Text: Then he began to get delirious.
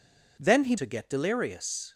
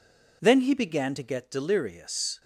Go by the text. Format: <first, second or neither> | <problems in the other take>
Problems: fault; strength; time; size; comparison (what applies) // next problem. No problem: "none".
second | skips "began"; at 0.7 s